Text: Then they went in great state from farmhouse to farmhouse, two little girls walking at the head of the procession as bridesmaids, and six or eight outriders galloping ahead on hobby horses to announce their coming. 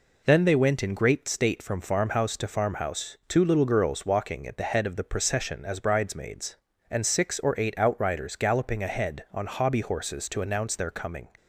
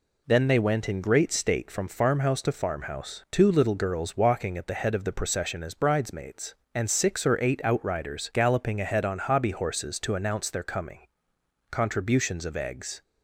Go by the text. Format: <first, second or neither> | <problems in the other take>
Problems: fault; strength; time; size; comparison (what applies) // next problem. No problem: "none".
first | goes on to say "Contributions of eggs"; from 11.7 s on; 1.3 s long